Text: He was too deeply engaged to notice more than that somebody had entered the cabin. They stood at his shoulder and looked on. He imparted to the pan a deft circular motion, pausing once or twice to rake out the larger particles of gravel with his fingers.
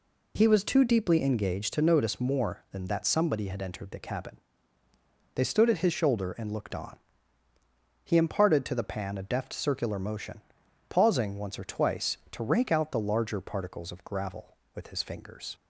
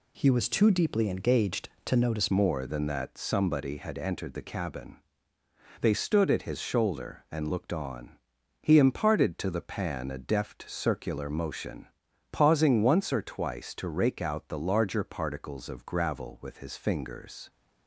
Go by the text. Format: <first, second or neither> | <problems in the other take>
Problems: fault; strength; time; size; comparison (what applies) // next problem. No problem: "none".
first | changes voice at "more"; from 2.2 s on; 15.2 s long